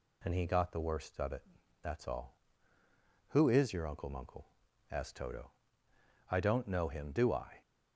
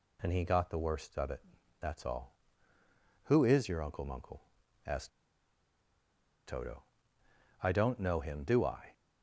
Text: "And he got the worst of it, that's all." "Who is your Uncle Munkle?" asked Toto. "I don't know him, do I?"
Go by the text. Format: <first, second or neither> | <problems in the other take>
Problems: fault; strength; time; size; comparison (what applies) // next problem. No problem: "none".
first | pauses between "asked" and "Toto"; strong; at 5.0 s; 1.3 s long